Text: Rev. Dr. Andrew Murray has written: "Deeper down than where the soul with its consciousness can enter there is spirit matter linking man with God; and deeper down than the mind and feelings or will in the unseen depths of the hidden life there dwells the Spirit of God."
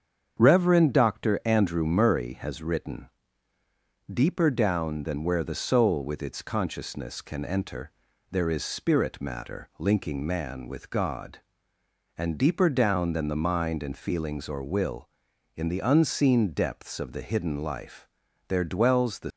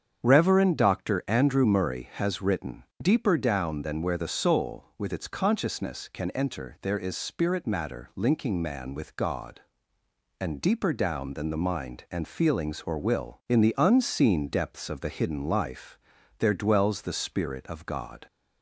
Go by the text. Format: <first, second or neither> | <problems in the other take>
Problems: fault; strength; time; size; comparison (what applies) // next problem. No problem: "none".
second | starts louder than the rest; strong; until 1.4 s; 7.5 dB; strong in the second // pauses between "enter" and "there"; at 7.8 s; 0.40 s long // pauses between "life" and "there"; at 18.0 s; 0.40 s long; also in the second // stops before "Spirit of God"; at 19.3 s